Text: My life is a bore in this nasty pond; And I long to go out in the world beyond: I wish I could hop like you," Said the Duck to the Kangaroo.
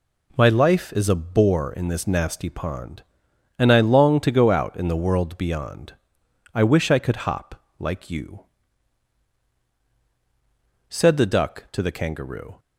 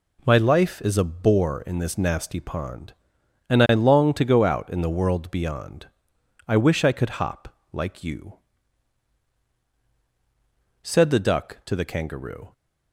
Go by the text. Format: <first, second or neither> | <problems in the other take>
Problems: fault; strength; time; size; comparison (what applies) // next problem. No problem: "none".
neither | pauses between "hop" and "like"; slight; the same in both